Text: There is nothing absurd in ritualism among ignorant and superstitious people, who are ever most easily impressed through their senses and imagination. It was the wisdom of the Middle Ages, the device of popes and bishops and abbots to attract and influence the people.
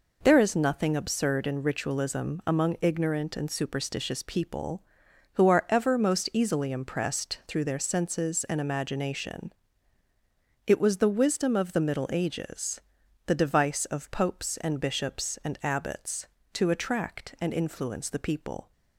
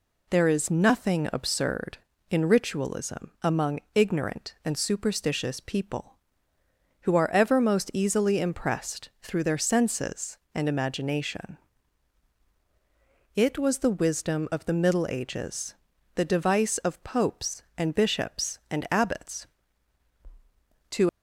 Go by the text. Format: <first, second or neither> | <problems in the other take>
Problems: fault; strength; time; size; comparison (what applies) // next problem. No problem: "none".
first | stops before "attract and influence the people"; at 21.0 s